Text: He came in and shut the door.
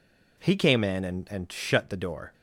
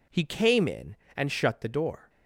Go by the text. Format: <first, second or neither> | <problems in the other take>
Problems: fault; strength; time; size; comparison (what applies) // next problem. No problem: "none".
second | says "and" twice; at 1.2 s